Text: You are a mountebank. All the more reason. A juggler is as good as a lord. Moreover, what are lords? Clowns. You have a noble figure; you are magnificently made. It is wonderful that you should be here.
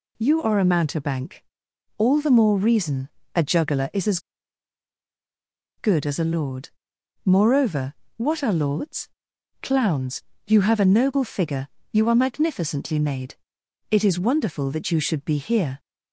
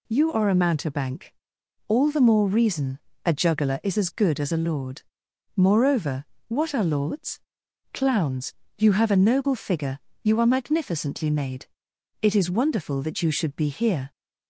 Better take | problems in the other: second | pauses between "as" and "good"; strong; at 4.1 s; 1.5 s long

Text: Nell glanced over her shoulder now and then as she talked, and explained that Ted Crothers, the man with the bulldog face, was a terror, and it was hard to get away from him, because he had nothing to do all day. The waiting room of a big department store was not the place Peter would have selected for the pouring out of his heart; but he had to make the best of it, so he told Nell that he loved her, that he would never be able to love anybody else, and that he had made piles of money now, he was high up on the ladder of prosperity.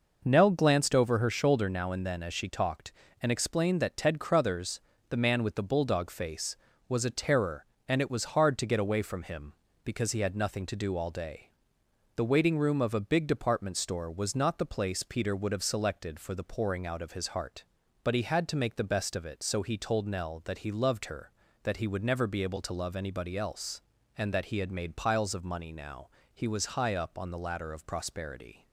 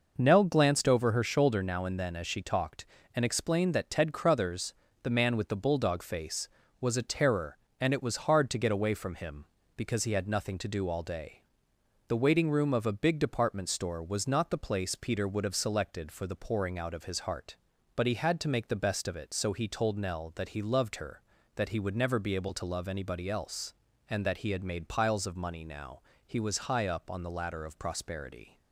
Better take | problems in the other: neither | none

